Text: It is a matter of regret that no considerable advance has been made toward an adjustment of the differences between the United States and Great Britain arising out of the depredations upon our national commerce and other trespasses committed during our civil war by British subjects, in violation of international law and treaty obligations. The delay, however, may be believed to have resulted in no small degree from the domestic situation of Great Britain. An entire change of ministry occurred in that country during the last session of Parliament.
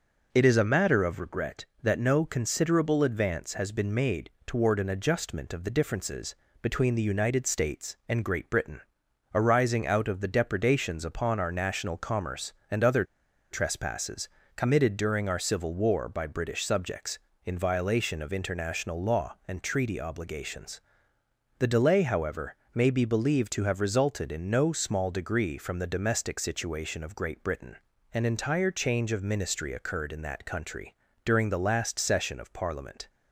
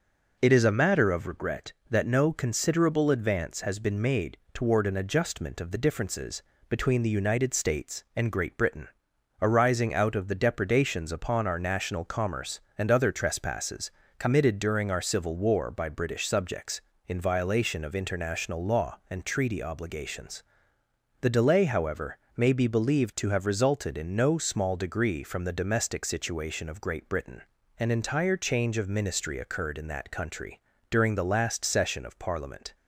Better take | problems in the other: second | pauses between "made" and "toward"; slight; at 4.3 s; 0.16 s long; slight in the second // pauses between "differences" and "between"; slight; at 6.3 s; 0.26 s long; slight in the second // pauses between "Britain" and "arising"; noticeable; at 8.8 s; 0.52 s long; noticeable in the second // pauses between "other" and "trespasses"; noticeable; at 13.0 s; 0.46 s long // pauses between "trespasses" and "committed"; slight; at 14.2 s; 0.28 s long; slight in the second // pauses between "country" and "during"; slight; at 30.9 s; 0.30 s long; slight in the second

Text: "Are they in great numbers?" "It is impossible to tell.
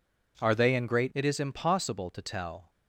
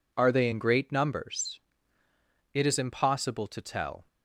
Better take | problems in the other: second | skips "numbers"; at 1.1 s

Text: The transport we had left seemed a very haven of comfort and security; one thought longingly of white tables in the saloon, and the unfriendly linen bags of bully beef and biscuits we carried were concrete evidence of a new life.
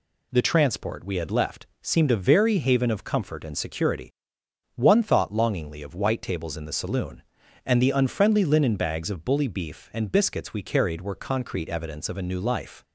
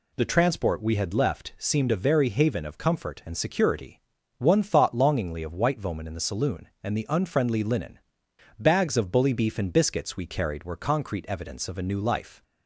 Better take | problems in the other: first | says "voman" for "tables"; at 5.8 s // pauses between "linen" and "bags"; noticeable; at 7.9 s; 0.62 s long

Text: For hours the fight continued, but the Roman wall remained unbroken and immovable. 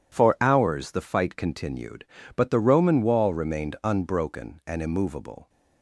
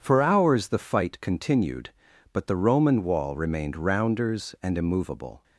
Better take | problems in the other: first | says "rounders" for "unbroken"; at 3.7 s

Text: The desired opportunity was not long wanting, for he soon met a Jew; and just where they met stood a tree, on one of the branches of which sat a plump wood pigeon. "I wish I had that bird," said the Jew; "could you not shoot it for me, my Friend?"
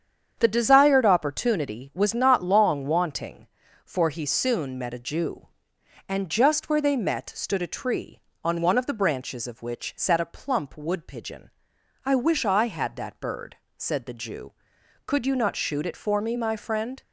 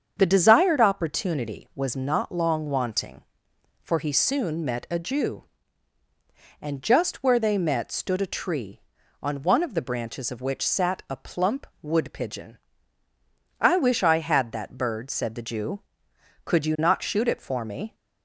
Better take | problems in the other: first | starts louder than the rest; strong; until 1.1 s; 7.5 dB; strong in the first // pauses between "plump" and "wood"; slight; at 11.6 s; 0.16 s long // stops before "my Friend"; at 17.9 s

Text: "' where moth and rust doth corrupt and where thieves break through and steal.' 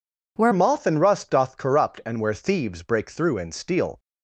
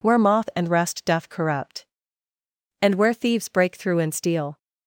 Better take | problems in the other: second | changes voice at "moth"; from 0.5 s on; 3.4 s long

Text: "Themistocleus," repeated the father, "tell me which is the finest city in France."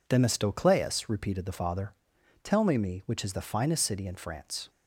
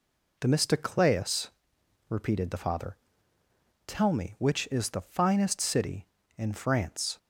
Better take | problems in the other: second | says "me" twice; at 2.7 s

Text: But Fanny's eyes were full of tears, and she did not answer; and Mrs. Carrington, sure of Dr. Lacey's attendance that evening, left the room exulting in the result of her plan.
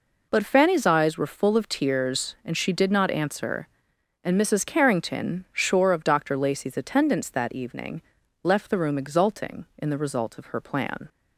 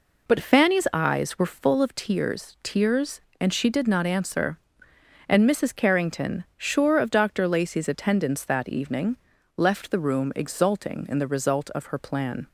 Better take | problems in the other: first | says "tears" twice; at 2.6 s

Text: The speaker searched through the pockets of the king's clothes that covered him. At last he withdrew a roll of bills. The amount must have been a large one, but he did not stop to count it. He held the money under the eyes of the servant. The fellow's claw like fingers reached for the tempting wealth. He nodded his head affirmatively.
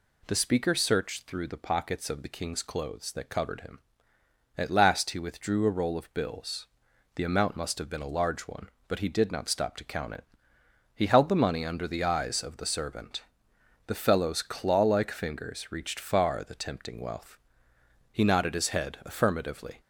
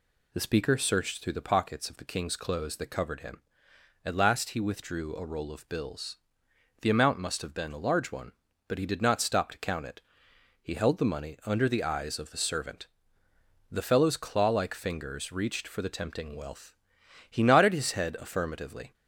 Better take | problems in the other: second | says "far" for "for"; at 15.9 s

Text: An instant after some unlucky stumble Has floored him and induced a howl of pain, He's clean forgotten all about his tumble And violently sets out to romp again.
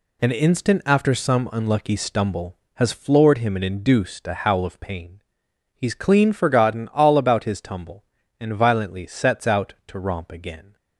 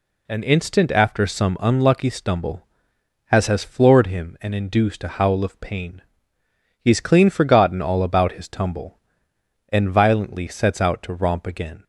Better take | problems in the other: first | says "Has" twice; at 3.4 s

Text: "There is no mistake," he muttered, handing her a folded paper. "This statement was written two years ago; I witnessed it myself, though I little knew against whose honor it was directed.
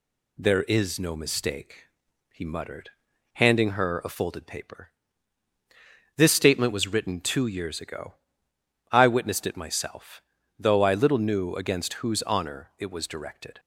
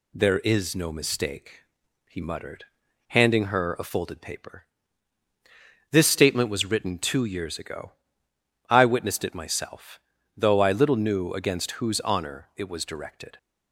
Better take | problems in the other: neither | none

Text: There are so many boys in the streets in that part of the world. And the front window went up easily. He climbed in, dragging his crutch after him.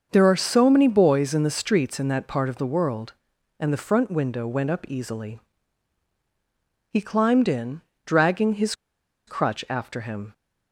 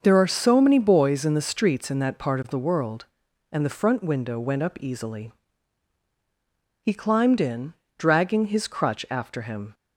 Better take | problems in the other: second | starts louder than the rest; until 1.1 s; 6.5 dB; also in the second // pauses between "his" and "crutch"; noticeable; at 8.7 s; 0.53 s long

